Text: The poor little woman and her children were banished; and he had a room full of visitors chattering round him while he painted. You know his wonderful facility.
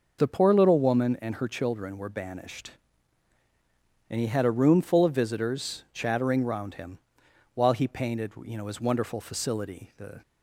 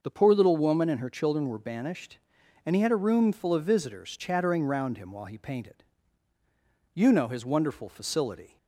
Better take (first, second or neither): second